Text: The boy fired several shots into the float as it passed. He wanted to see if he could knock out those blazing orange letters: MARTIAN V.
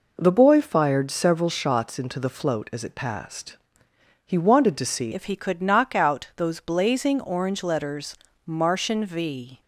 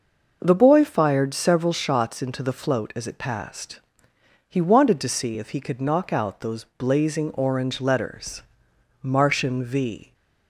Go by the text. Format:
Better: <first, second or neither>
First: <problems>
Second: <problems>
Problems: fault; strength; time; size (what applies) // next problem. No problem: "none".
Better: second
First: changes voice at "if"; from 5.1 s on; 4.5 s long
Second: none